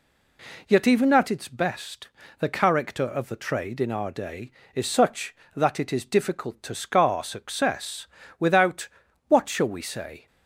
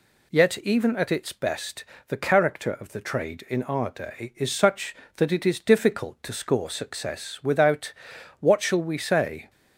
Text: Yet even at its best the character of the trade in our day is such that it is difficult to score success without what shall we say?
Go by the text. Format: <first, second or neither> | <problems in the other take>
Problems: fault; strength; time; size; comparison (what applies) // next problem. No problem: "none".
second | pauses between "best" and "the"; slight; at 2.0 s; 0.30 s long; slight in the second // says "scar" for "score"; at 6.7 s // pauses between "success" and "without"; slight; at 8.0 s; 0.32 s long // pauses between "without" and "what"; at 8.8 s; 0.40 s long; noticeable in the second